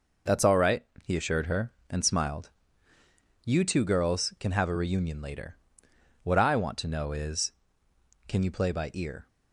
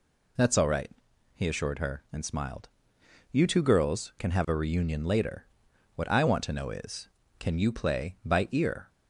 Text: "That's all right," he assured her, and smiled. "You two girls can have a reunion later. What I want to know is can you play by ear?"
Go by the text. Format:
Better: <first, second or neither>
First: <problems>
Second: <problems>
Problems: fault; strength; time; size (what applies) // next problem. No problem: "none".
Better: neither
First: none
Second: none